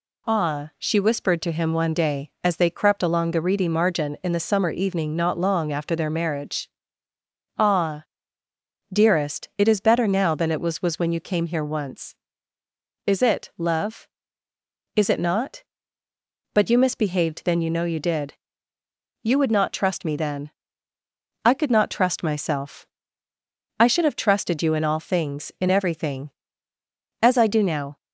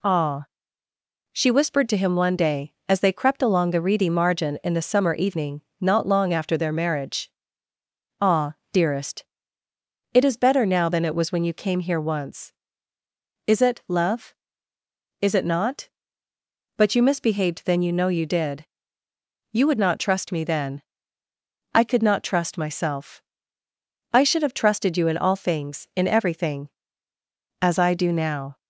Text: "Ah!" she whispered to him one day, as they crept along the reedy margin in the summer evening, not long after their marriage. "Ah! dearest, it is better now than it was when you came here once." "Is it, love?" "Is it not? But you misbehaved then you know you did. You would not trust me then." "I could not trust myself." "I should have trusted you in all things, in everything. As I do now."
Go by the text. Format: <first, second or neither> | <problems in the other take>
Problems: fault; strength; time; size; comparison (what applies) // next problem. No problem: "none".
second | says "was" twice; at 10.8 s